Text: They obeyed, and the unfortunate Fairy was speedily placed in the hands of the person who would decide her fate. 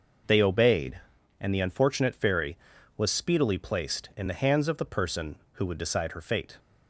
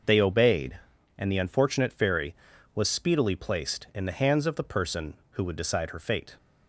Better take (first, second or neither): neither